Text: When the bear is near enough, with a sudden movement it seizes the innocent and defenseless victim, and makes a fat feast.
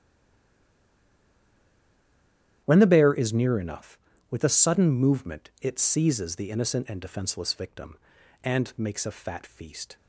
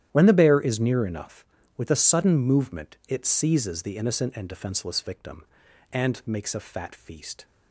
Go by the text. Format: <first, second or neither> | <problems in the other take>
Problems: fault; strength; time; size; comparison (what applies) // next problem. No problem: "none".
second | stays silent before the first word; strong; until 2.6 s; 2.6 s long // starts louder than the rest; strong; until 3.6 s; 11 dB; strong in the second